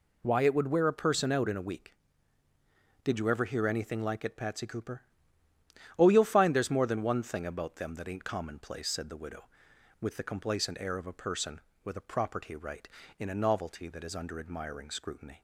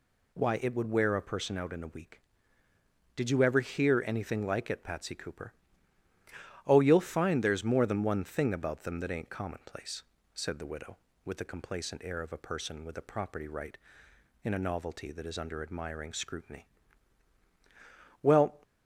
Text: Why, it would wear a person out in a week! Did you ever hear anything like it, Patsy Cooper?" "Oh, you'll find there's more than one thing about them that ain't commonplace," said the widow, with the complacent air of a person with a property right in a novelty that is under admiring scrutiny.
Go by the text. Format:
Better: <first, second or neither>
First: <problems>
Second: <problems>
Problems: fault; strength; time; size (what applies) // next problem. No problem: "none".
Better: first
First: none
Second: goes on to say "Well"; slight; from 18.2 s on; 0.40 s long